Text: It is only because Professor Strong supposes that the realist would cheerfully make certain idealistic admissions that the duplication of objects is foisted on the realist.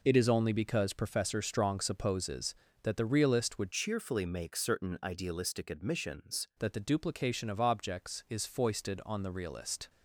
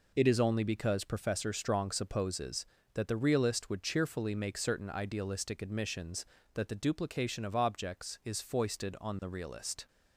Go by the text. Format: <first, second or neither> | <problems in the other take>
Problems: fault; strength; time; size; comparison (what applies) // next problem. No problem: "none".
second | changes voice from "cheerfully" to "admissions"; from 3.7 to 6.4 s; 2.7 s long